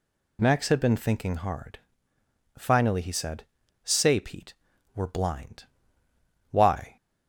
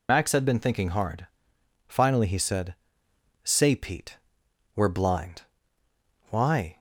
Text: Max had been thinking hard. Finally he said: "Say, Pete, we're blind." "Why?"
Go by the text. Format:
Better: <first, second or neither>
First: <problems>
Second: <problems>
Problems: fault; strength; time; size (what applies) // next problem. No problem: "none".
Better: first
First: none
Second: loses the start of "Max"; at 0.0 s; 105 ms